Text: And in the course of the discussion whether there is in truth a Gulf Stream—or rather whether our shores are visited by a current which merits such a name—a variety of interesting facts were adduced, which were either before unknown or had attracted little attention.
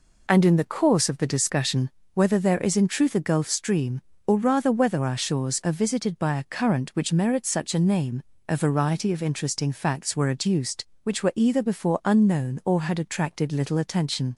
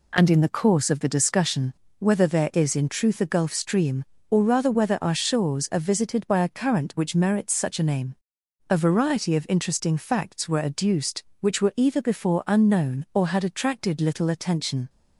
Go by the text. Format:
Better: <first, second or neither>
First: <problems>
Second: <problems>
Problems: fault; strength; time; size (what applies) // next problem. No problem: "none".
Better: neither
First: pauses between "discussion" and "whether"; slight; at 1.8 s; 0.26 s long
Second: pauses between "discussion" and "whether"; slight; at 1.7 s; 0.25 s long